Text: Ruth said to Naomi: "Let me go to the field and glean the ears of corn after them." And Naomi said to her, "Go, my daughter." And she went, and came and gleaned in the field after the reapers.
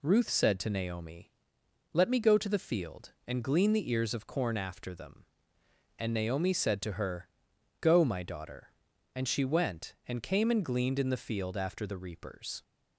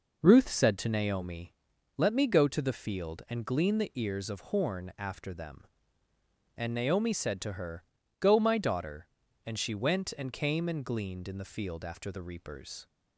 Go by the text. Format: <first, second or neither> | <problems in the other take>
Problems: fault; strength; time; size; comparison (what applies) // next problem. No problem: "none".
first | says "horn" for "corn"; at 4.4 s